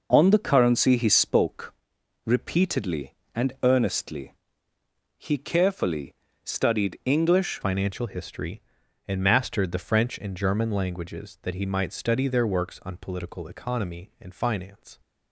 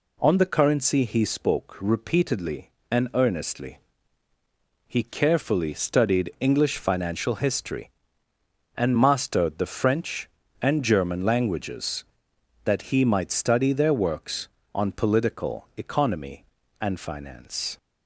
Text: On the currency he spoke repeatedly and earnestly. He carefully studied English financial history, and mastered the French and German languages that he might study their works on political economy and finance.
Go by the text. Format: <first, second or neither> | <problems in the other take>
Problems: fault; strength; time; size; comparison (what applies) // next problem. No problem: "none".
second | pauses between "spoke" and "repeatedly"; noticeable; at 1.7 s; 0.52 s long // pauses between "carefully" and "studied"; slight; at 6.1 s; 0.28 s long // changes voice at "financial"; from 7.6 s on; 7.3 s long